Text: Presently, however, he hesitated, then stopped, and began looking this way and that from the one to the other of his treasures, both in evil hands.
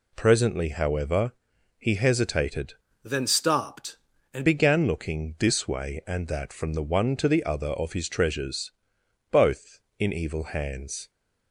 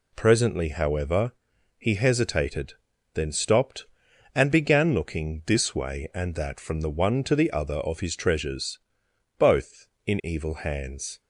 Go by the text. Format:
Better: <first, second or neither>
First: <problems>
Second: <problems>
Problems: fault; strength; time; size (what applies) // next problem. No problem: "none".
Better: second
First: changes voice from "then" to "and"; from 3.0 to 4.4 s; 1.4 s long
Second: none